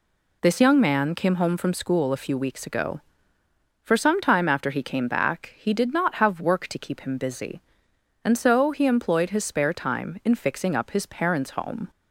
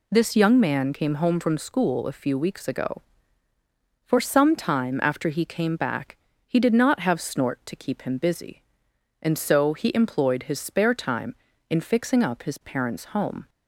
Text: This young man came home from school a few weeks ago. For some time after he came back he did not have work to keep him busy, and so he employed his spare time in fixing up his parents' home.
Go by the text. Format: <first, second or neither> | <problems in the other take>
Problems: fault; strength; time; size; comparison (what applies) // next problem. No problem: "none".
first | pauses between "back" and "he"; slight; at 6.1 s; 0.30 s long // says "snort" for "work"; at 7.2 s